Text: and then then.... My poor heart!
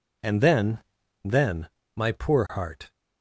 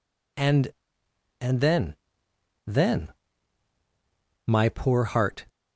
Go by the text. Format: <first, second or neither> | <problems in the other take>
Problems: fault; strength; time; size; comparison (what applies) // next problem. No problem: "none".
first | says "and" twice; at 1.4 s // pauses between "then" and "then"; noticeable; at 1.9 s; 0.73 s long; also in the first